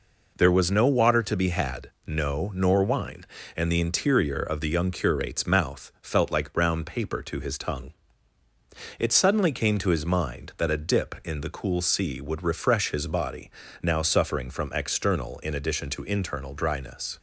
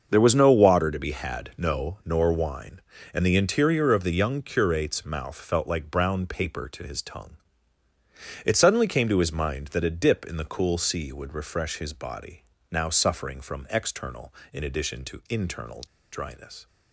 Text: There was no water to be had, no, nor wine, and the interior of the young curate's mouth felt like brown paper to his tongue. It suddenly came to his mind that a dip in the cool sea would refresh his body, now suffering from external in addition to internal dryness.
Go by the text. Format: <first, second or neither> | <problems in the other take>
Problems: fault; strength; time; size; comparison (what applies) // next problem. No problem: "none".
first | starts louder than the rest; until 1.1 s; 6.5 dB // pauses between "internal" and "dryness"; slight; at 15.8 s; 0.31 s long